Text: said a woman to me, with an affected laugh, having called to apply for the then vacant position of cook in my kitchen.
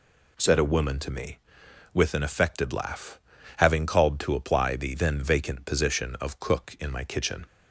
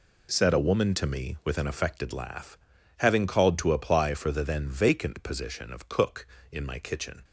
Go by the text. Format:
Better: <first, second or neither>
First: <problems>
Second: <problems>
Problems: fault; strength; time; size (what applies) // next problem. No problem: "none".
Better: second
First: skips "for"; at 4.7 s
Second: none